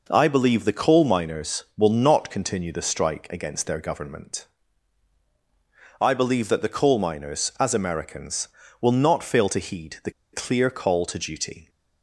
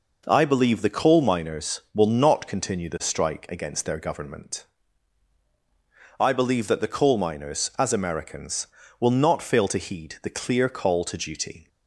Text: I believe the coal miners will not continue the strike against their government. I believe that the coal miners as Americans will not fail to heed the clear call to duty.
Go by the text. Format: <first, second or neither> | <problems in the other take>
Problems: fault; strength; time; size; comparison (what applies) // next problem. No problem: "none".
second | pauses between "the" and "clear"; slight; at 10.1 s; 0.21 s long